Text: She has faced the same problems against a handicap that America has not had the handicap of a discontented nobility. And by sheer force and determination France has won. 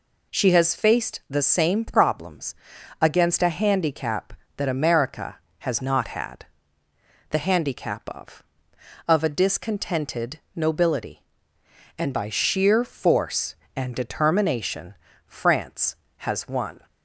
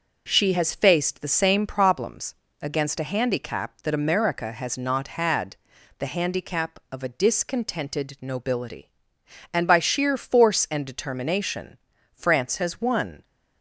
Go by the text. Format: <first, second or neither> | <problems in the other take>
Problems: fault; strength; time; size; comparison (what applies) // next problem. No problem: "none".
second | pauses between "problems" and "against"; noticeable; at 2.5 s; 0.46 s long; slight in the second // pauses between "had" and "the"; noticeable; at 6.4 s; 0.86 s long; also in the second // says "of" twice; at 9.0 s // pauses between "discontented" and "nobility"; slight; at 10.3 s; 0.16 s long // pauses between "determination" and "France"; slight; at 14.9 s; 0.34 s long; also in the second